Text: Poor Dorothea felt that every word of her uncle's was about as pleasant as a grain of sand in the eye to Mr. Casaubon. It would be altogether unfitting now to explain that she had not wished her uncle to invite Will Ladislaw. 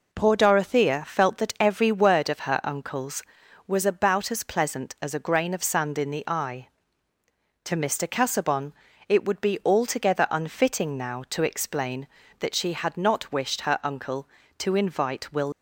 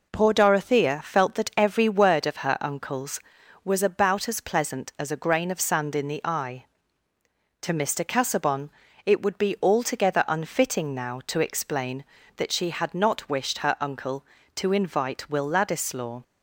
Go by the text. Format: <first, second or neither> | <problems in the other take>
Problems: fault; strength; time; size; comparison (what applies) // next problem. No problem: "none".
second | stops before "Ladislaw"; at 15.5 s